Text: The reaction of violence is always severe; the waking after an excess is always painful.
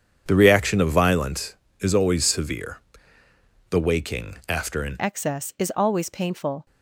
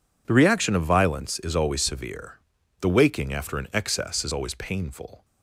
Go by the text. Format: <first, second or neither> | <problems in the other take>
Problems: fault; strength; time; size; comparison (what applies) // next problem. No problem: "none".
second | changes voice at "excess"; from 5.0 s on; 1.6 s long